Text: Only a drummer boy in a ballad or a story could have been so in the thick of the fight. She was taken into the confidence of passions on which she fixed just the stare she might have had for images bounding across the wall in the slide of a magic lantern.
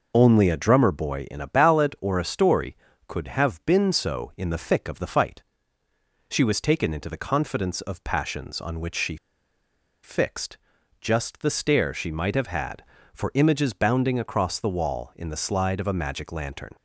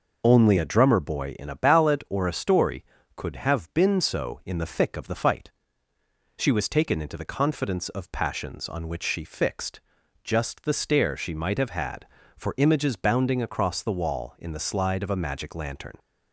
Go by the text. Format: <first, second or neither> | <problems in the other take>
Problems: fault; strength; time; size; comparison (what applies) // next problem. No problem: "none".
second | pauses between "she" and "fixed"; noticeable; at 9.1 s; 0.86 s long // pauses between "fixed" and "just"; at 10.5 s; 0.44 s long; also in the second